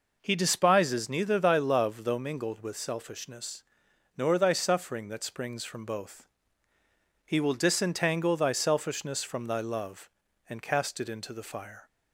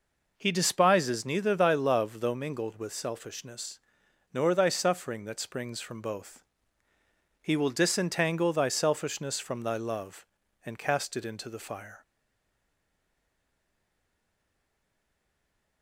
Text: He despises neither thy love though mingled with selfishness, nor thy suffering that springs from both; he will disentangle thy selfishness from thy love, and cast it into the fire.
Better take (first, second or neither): first